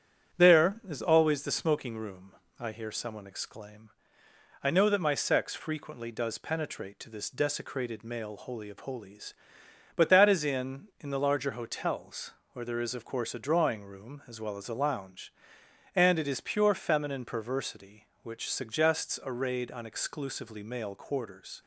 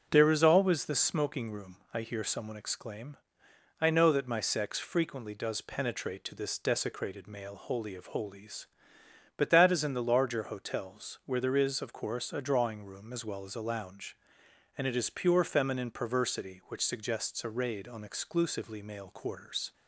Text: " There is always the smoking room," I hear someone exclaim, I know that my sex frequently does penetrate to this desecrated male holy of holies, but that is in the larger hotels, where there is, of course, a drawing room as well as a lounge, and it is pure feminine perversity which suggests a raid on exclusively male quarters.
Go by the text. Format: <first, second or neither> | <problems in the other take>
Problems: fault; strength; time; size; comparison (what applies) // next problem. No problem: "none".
second | starts louder than the rest; strong; until 1.4 s; 9 dB; also in the second // says "in" twice; at 10.9 s